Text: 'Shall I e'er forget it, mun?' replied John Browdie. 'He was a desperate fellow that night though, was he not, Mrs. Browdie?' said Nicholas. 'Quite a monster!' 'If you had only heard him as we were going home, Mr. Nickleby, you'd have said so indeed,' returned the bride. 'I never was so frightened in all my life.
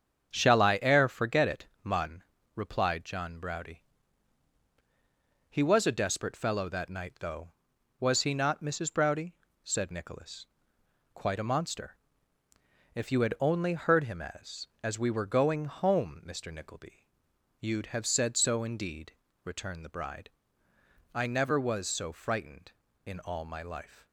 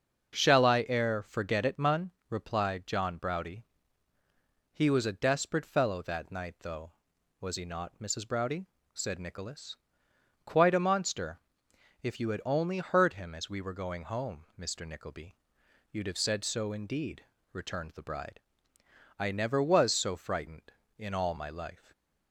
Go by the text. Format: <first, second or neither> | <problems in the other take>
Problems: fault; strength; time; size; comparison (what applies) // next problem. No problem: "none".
second | starts louder than the rest; strong; until 1.3 s; 7.5 dB; also in the second // says "as" twice; at 14.8 s